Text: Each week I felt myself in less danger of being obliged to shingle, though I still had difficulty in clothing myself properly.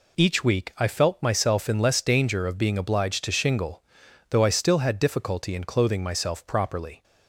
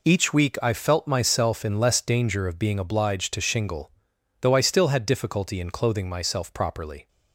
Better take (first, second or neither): neither